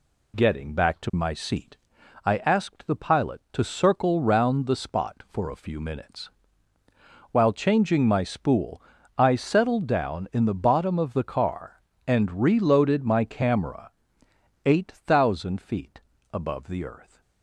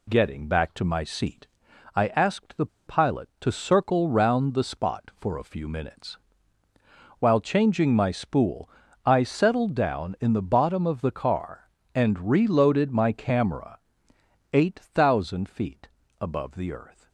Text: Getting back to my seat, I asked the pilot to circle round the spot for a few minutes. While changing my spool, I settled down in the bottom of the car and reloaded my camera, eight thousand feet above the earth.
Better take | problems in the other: first | pauses between "the" and "pilot"; slight; at 2.6 s; 0.20 s long // pauses between "feet" and "above"; slight; at 15.8 s; 0.32 s long; slight in the first

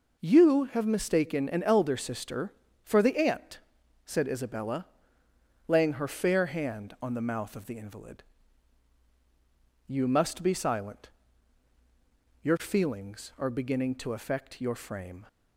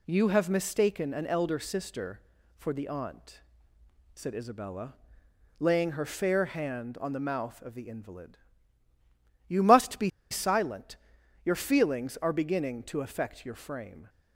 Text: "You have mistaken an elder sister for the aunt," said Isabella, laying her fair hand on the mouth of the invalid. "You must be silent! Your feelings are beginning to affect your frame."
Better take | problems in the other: first | pauses between "be" and "silent"; slight; at 10.1 s; 0.20 s long

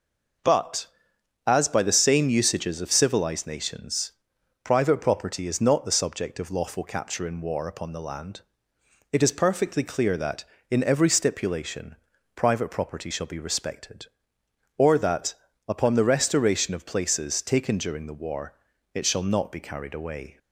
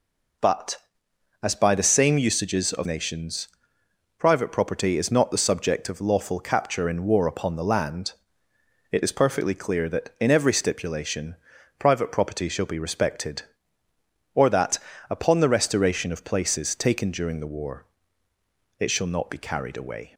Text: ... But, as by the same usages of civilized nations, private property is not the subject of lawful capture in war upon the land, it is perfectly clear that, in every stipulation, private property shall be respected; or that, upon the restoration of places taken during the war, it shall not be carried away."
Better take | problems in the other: first | skips "civilized"; at 2.8 s

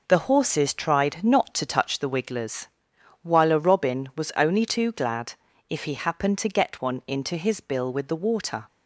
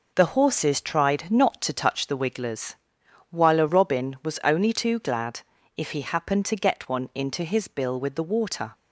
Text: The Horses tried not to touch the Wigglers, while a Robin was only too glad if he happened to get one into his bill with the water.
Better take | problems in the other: neither | pauses between "glad" and "if"; slight; the same in both

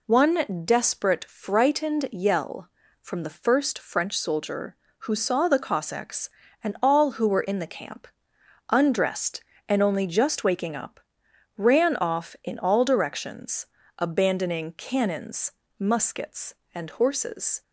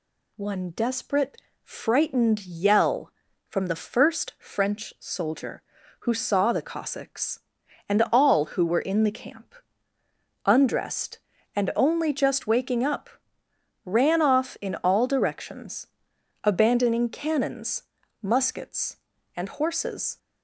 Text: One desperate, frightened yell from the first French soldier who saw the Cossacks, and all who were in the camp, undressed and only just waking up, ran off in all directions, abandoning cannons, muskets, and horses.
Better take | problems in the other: neither | none

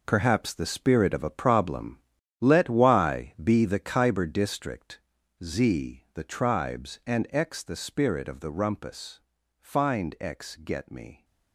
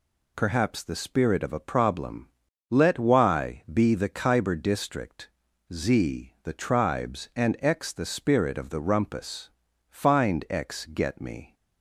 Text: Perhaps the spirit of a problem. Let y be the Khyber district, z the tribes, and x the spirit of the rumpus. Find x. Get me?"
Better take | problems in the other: second | gets quieter; strong; throughout; 12 dB

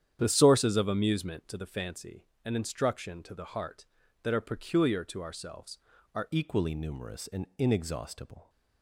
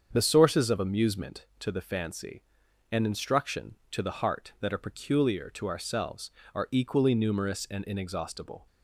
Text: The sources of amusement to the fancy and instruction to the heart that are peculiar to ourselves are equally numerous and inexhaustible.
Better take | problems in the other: second | starts louder than the rest; strong; until 1.2 s; 9.5 dB; strong in the second // changes voice at "equally"; from 6.3 s on; 2.1 s long

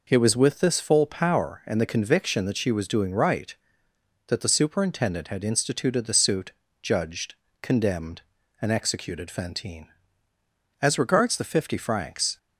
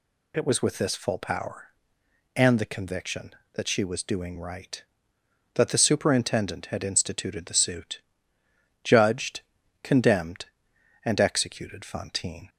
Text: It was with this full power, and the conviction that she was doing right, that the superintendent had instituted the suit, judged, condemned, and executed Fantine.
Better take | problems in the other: second | goes on to say "As regards the fifty francs"; from 10.8 s on; 1.5 s long

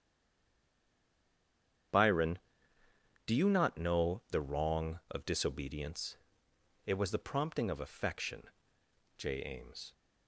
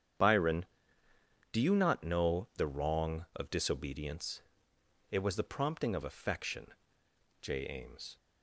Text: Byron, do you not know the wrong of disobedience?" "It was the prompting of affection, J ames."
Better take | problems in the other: second | stays silent before the first word; noticeable; until 1.9 s; 1.9 s long // starts louder than the rest; strong; until 3.8 s; 8.5 dB; strong in the second

